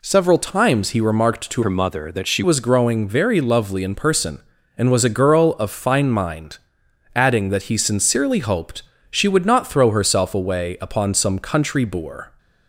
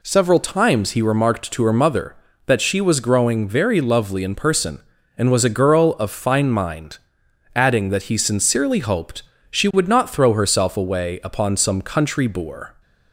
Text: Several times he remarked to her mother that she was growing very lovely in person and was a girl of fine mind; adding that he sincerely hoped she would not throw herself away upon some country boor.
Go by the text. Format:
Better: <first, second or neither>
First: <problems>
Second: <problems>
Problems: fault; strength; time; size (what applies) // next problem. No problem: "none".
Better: second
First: changes voice from "her" to "she"; from 1.6 to 2.4 s; 0.8 s long // pauses between "hoped" and "she"; slight; at 8.8 s; 0.26 s long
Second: pauses between "hoped" and "she"; slight; at 9.2 s; 0.26 s long